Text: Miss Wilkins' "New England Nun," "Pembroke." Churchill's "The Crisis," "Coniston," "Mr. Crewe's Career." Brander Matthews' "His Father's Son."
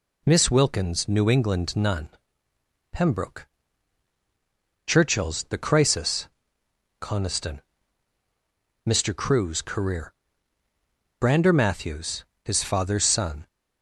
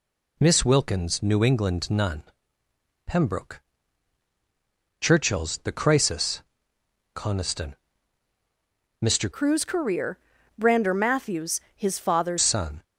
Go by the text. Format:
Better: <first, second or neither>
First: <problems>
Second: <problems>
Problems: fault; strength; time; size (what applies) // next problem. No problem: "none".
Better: first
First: pauses between "Matthews" and "His"; slight; at 12.2 s; 0.20 s long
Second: changes voice from "Crewe's" to "Father's"; from 9.3 to 12.3 s; 3.0 s long // pauses between "Matthews" and "His"; slight; at 11.6 s; 0.16 s long